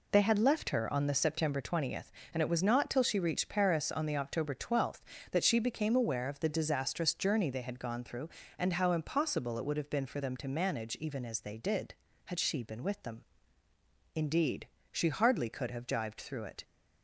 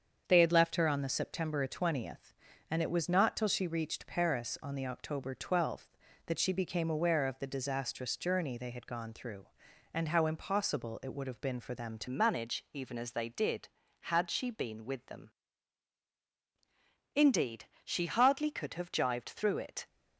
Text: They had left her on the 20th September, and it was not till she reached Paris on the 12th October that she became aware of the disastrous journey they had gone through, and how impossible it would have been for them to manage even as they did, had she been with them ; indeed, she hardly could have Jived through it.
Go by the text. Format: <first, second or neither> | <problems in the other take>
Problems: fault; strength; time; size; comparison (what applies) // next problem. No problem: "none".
first | starts louder than the rest; strong; until 1.2 s; 7 dB // changes voice at "manage"; from 12.0 s on; 7.8 s long